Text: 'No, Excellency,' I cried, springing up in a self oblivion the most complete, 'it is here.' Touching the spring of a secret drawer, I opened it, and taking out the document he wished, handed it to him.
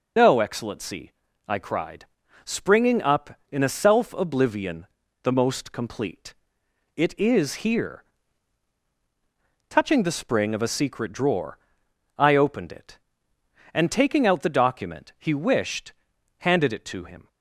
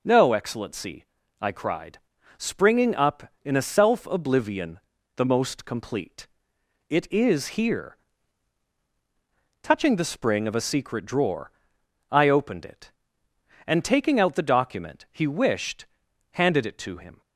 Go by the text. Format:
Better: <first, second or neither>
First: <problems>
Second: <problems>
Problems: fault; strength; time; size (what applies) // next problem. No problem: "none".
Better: second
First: loses the start of "No"; at 0.1 s; 65 ms // pauses between "oblivion" and "the"; slight; at 4.8 s; 0.36 s long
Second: pauses between "oblivion" and "the"; slight; at 4.7 s; 0.36 s long